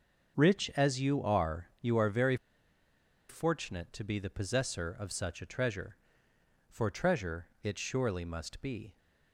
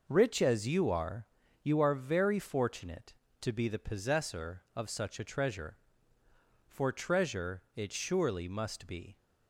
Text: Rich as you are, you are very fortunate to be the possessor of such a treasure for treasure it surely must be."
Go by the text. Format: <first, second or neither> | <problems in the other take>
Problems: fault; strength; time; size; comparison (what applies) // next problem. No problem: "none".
second | starts louder than the rest; until 1.4 s; 6.5 dB // pauses between "very" and "fortunate"; noticeable; at 2.3 s; 0.93 s long // pauses between "treasure" and "it"; slight; at 7.4 s; 0.16 s long